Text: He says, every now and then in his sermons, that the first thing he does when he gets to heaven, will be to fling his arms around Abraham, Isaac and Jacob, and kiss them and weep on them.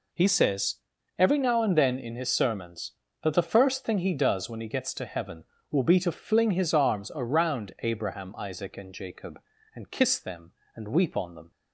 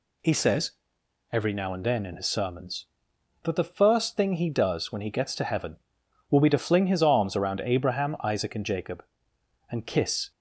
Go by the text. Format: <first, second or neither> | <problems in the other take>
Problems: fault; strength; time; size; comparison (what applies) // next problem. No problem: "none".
first | stops before "them and weep on them"; at 10.3 s